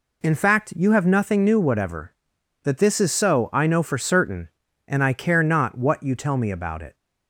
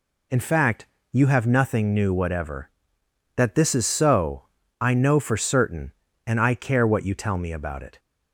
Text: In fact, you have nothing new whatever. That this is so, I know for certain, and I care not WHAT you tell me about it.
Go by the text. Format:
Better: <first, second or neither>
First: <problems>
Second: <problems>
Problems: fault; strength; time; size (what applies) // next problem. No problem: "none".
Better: first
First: none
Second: skips "not"; at 6.8 s